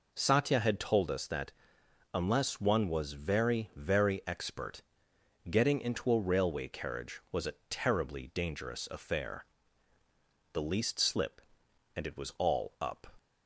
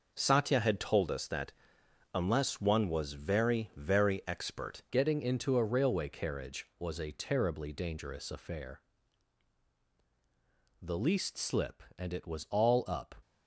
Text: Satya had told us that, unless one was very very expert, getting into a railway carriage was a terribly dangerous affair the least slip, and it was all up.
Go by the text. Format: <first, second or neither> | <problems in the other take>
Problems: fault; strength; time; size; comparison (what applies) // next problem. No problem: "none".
first | changes voice at "getting"; from 4.9 s on; 8.2 s long // pauses between "affair" and "the"; strong; at 8.8 s; 2.0 s long; also in the first